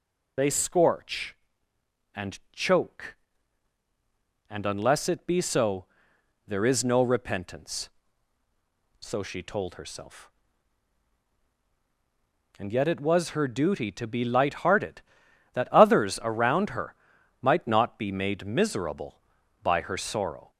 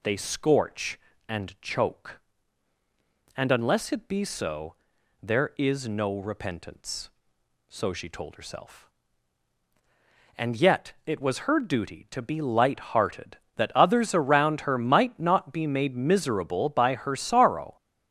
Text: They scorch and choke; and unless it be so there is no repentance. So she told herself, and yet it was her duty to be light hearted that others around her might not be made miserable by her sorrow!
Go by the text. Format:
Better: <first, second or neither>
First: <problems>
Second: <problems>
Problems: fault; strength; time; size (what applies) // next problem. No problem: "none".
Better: second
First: loses the start of "They"; at 0.3 s; 75 ms // pauses between "so" and "there"; noticeable; at 5.8 s; 0.60 s long // pauses between "her" and "might"; noticeable; at 16.9 s; 0.46 s long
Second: pauses between "so" and "there"; noticeable; at 4.7 s; 0.48 s long